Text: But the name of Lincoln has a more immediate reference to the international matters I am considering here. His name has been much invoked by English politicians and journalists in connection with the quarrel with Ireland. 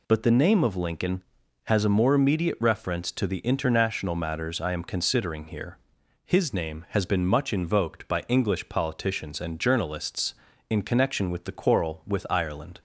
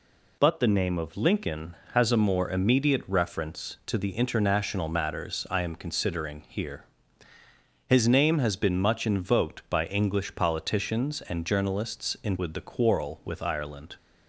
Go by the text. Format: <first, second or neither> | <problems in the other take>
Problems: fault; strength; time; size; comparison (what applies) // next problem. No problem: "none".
first | skips "connection"; at 12.3 s